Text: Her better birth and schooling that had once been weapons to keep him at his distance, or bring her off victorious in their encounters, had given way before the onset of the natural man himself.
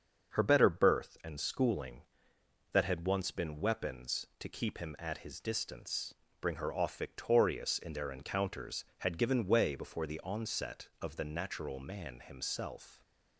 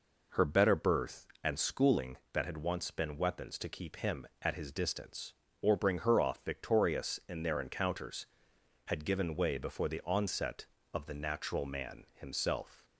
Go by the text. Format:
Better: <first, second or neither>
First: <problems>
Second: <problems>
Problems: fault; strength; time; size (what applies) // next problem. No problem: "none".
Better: second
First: starts louder than the rest; until 1.3 s; 6.5 dB // skips "or"; at 6.2 s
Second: none